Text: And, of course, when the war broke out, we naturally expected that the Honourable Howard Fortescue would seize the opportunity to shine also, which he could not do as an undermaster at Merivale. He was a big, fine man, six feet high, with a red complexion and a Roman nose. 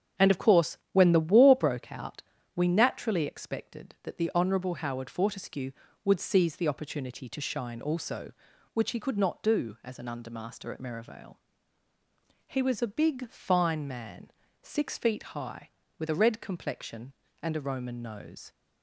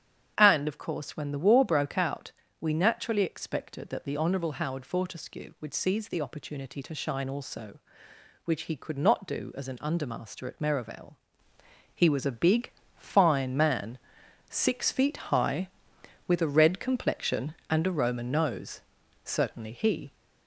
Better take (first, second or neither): first